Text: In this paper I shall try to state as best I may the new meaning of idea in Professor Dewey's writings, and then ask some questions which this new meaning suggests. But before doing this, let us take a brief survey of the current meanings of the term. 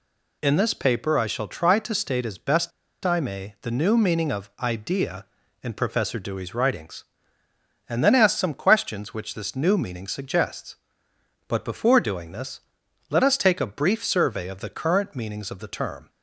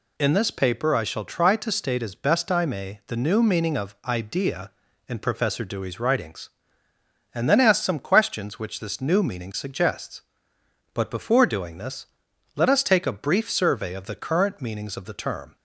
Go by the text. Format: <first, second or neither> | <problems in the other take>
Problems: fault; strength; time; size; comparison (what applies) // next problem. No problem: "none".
second | pauses between "best" and "I"; slight; at 2.7 s; 0.34 s long